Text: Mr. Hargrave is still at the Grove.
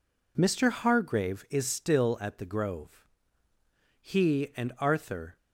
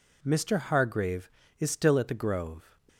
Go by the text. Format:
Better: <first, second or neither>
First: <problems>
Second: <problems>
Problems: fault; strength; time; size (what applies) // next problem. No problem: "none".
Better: second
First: goes on to say "He and Arthur"; from 4.0 s on; 1.3 s long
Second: none